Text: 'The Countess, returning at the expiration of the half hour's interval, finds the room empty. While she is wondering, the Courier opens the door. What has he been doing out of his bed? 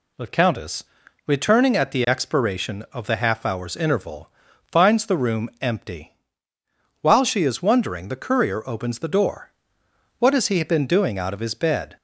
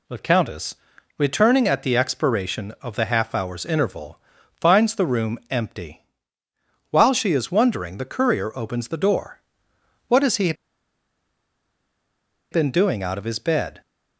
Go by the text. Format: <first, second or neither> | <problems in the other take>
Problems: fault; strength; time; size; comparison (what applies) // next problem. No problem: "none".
first | pauses between "he" and "been"; strong; at 10.5 s; 2.0 s long